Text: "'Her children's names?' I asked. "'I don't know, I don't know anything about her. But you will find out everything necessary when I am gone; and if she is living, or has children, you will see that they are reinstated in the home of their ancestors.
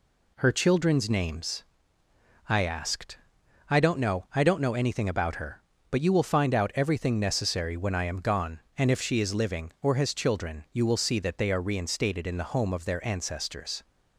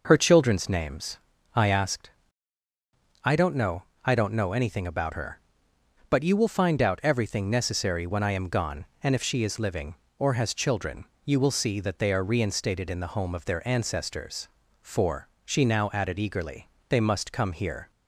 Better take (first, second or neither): first